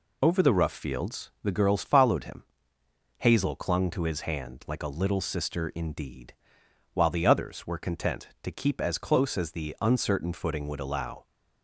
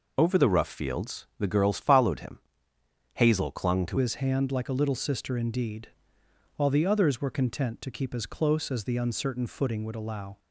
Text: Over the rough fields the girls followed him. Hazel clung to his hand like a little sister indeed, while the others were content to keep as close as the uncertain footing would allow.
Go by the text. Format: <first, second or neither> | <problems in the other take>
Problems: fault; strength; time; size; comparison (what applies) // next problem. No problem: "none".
first | changes voice at "his"; from 3.9 s on; 6.4 s long